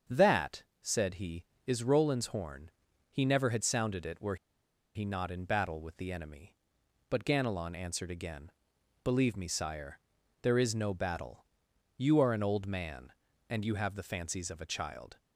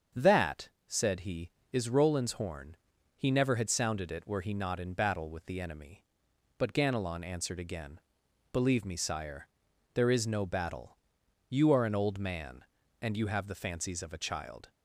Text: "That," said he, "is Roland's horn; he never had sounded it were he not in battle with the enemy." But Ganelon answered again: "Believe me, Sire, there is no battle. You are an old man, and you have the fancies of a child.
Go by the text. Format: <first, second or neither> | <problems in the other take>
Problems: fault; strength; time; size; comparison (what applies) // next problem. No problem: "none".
second | starts louder than the rest; until 1.2 s; 7 dB; also in the second // pauses between "were" and "he"; noticeable; at 4.3 s; 0.58 s long